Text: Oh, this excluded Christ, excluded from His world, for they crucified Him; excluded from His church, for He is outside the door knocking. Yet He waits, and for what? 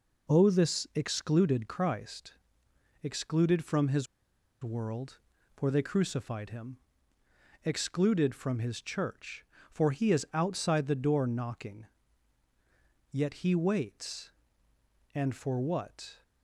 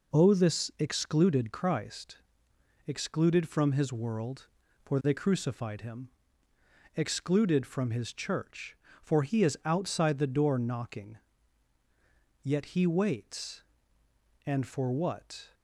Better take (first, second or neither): second